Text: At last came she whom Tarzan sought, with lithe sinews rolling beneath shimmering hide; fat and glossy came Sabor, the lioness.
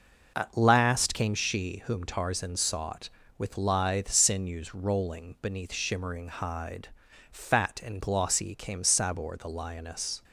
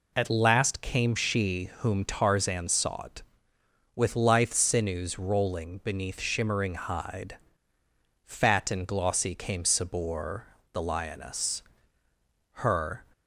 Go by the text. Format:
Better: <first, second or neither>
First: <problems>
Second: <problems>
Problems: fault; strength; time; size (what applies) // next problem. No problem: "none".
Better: first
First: none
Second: goes on to say "Her"; from 12.5 s on; 0.54 s long